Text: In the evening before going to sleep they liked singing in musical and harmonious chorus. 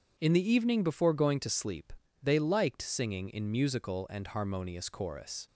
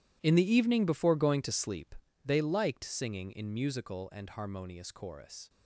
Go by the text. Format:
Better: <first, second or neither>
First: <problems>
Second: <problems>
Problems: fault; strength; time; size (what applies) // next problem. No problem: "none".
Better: first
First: pauses between "sleep" and "they"; slight; at 1.9 s; 0.30 s long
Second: gets quieter; strong; throughout; 16.5 dB // pauses between "sleep" and "they"; slight; at 1.9 s; 0.30 s long